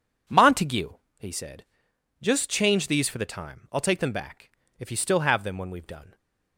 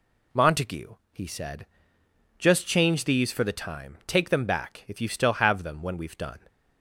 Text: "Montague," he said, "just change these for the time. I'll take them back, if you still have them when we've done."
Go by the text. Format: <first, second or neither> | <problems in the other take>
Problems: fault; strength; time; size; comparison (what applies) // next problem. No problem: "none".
first | skips "I'll"; at 4.0 s